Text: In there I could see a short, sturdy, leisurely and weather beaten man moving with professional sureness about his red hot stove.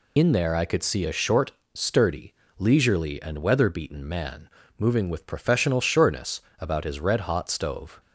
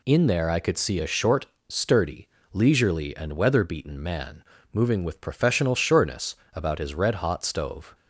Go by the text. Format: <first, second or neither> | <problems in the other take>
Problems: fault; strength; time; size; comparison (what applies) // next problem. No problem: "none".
second | loses the start of "In"; at 0.1 s; 65 ms // pauses between "man" and "moving"; slight; at 4.4 s; 0.30 s long; slight in the second // pauses between "sureness" and "about"; slight; at 6.3 s; 0.20 s long; slight in the second